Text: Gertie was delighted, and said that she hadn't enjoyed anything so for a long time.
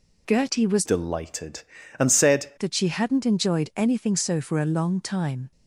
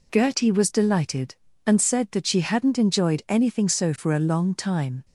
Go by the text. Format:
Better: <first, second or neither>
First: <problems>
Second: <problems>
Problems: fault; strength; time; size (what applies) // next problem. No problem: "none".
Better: second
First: changes voice from "delighted" to "said"; from 0.8 to 2.5 s; 1.7 s long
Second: none